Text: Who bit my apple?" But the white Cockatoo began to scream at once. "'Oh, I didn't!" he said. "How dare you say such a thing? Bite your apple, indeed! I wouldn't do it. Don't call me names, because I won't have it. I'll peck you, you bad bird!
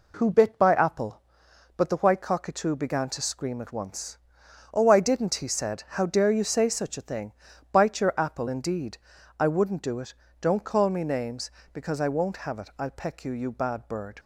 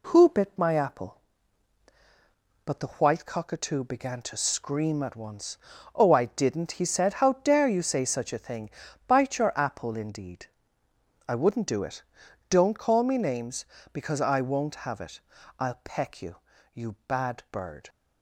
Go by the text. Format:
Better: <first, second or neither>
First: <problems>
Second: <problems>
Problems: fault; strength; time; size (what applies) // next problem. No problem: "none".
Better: second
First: says "by" for "my"; at 0.5 s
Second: none